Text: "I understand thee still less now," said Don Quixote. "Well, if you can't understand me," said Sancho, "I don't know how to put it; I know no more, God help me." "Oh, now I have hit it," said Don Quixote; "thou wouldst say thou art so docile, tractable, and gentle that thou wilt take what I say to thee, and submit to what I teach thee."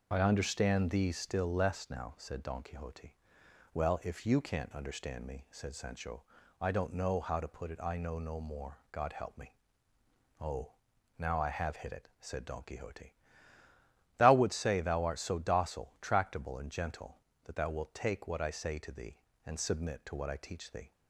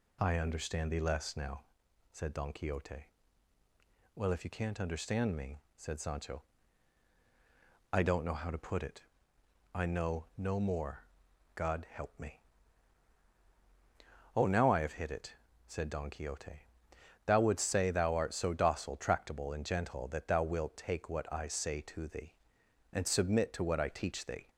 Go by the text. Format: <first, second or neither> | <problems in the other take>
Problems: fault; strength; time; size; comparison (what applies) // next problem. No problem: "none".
first | skips "still"; at 0.9 s